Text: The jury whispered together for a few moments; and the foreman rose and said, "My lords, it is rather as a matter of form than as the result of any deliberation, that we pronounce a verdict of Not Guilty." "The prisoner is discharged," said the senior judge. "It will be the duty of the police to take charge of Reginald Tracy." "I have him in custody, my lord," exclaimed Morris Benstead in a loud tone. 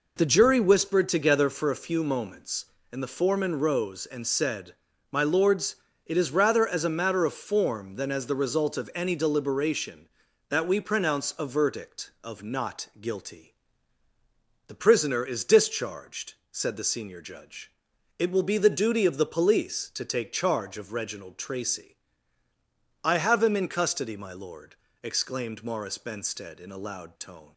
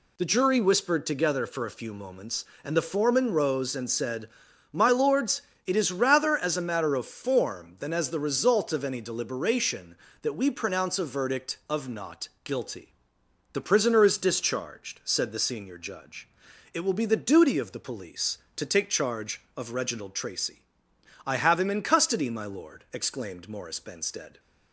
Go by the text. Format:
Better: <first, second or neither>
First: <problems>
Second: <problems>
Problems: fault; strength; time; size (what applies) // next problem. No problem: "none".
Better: first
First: none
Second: pauses between "Not" and "Guilty"; slight; at 12.2 s; 0.16 s long // stops before "in a loud tone"; at 24.3 s